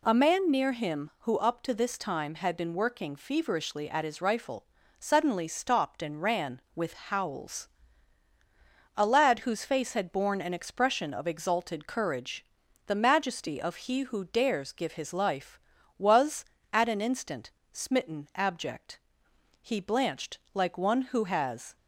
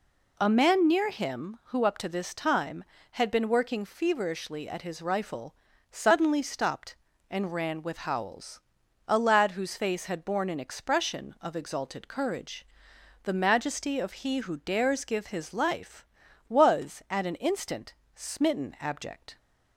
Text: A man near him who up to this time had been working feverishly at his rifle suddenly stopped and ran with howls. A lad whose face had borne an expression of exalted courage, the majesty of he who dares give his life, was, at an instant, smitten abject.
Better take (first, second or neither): second